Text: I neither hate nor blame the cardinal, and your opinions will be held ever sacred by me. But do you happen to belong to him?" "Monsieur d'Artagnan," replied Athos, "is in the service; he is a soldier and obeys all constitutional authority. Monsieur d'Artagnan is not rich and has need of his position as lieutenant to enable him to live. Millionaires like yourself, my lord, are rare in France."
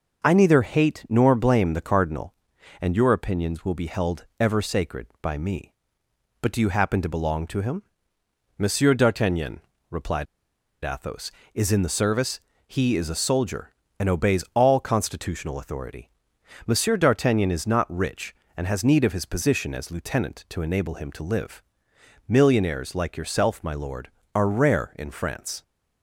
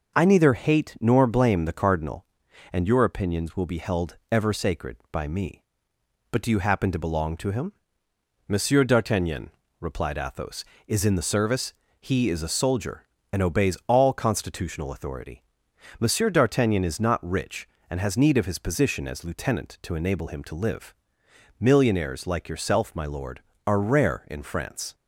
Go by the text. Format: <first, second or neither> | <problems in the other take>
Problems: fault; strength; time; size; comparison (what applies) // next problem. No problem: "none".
second | pauses between "replied" and "Athos"; noticeable; at 10.2 s; 0.58 s long